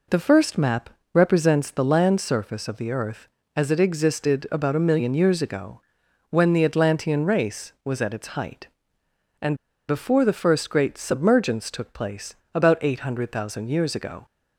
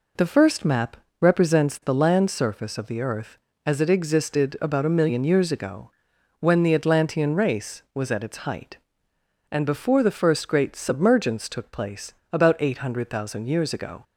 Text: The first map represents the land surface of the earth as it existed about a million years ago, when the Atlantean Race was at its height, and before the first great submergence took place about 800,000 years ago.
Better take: second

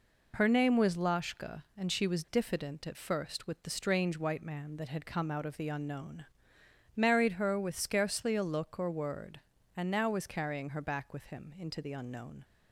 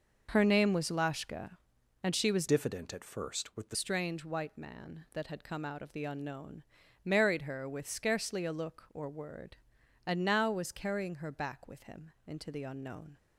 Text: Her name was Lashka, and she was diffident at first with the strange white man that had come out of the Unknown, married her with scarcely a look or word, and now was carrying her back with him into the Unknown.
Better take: first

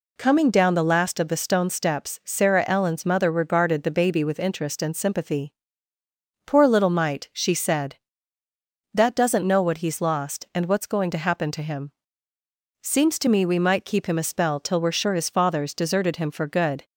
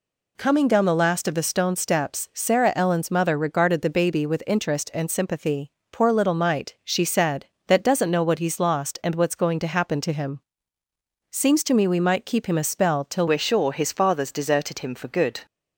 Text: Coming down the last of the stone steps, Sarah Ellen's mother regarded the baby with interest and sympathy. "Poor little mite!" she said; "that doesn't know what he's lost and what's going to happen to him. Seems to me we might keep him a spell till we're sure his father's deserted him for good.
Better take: first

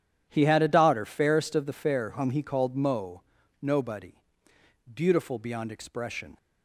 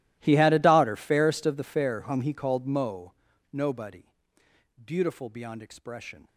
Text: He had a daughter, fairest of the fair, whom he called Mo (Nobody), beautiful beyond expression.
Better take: first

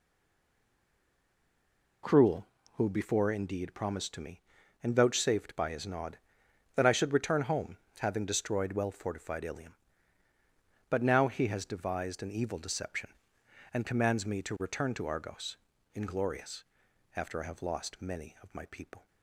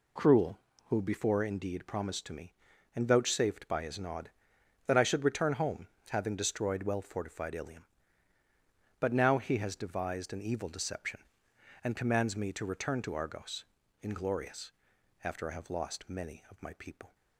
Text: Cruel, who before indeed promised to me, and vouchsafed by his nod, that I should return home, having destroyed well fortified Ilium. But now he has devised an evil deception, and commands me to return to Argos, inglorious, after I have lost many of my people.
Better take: second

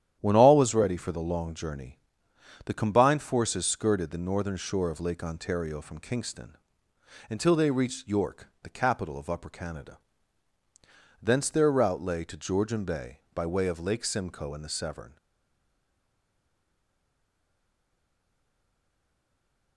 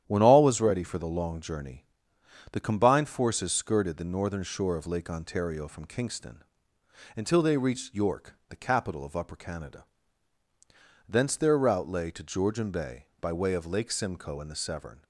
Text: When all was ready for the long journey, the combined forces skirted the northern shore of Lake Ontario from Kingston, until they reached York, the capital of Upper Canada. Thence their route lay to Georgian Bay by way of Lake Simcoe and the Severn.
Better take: second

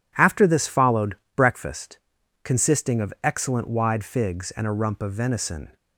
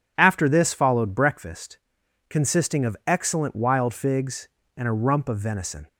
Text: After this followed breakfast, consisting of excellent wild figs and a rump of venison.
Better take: second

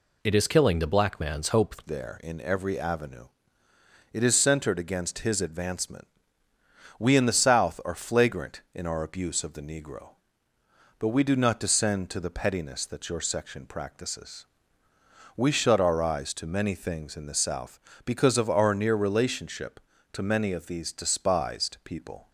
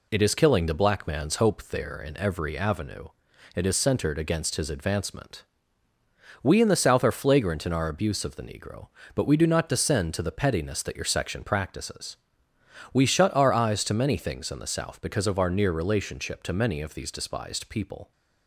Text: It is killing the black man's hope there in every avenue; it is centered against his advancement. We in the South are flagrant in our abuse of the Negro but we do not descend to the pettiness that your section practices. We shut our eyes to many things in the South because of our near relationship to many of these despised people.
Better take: second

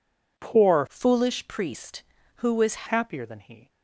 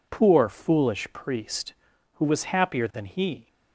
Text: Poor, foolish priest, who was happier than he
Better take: second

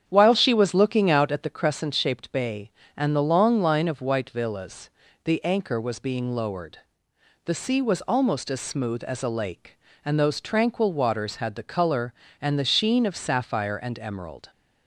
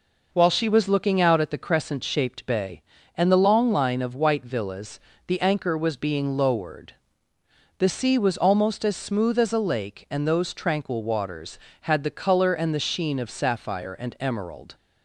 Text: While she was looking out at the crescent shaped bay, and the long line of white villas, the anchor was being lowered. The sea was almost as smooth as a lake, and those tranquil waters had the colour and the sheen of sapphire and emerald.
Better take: second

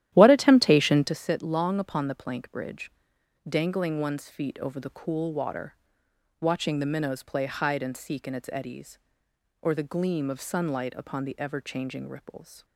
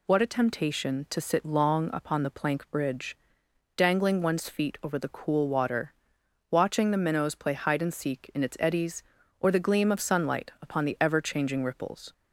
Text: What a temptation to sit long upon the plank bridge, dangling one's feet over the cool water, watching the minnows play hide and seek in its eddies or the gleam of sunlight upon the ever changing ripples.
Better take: second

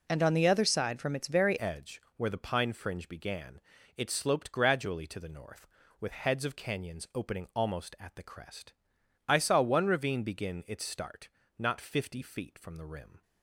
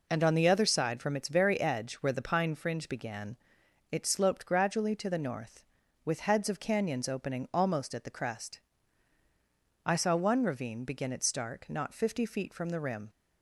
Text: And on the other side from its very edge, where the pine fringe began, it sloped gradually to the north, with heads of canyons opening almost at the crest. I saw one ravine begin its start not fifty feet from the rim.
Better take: second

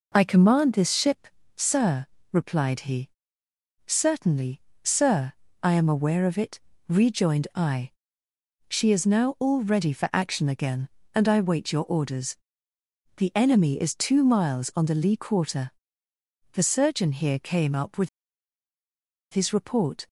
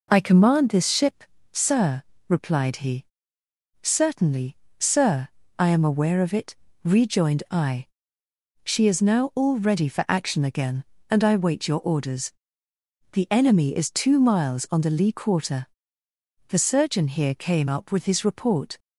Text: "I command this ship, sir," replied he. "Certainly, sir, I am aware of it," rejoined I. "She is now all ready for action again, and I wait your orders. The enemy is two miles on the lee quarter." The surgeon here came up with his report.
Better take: second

